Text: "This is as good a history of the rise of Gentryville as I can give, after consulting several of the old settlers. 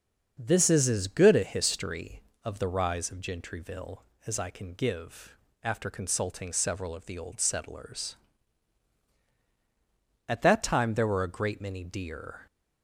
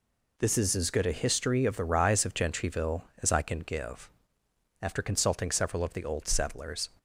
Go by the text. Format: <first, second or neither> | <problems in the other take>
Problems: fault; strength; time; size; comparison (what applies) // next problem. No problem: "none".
second | starts louder than the rest; until 1.3 s; 6.5 dB // goes on to say "At that time there were a great many deer"; strong; from 10.2 s on; 2.1 s long